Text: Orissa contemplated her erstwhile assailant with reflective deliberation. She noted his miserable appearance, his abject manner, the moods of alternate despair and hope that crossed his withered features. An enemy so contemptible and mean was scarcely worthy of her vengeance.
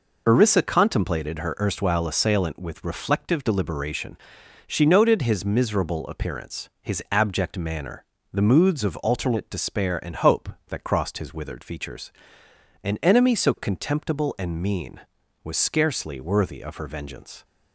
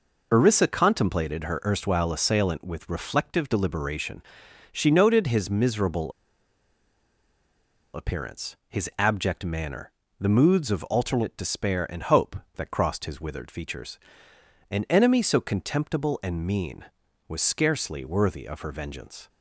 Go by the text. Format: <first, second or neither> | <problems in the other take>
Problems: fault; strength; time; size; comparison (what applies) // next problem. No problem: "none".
first | pauses between "miserable" and "appearance"; strong; at 6.1 s; 1.8 s long